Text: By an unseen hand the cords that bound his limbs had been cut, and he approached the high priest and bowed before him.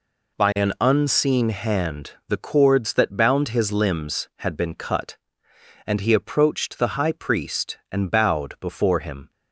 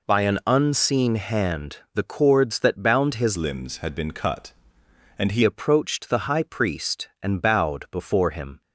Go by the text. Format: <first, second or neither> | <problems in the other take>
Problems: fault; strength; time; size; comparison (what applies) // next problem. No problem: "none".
first | pauses between "hand" and "the"; slight; at 1.7 s; 0.18 s long; slight in the first // changes voice from "limbs" to "he"; from 3.3 to 5.4 s; 2.1 s long